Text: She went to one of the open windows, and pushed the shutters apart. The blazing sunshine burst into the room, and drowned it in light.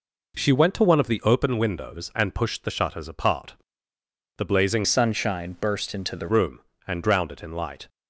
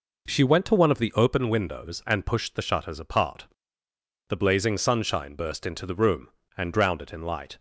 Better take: second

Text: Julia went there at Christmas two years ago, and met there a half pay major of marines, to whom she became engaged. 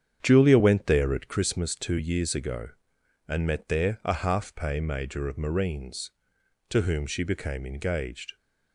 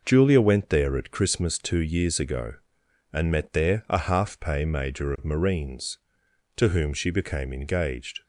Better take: second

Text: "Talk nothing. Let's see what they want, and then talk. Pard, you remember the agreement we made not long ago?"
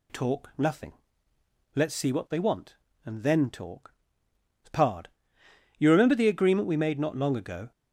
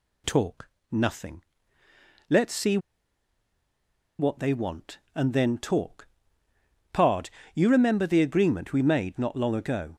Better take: first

